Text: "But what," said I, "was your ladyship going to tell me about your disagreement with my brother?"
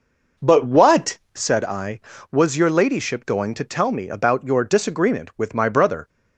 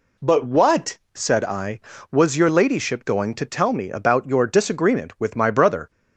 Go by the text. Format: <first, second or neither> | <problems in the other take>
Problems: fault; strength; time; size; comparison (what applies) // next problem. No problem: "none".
second | starts louder than the rest; noticeable; until 1.5 s; 5 dB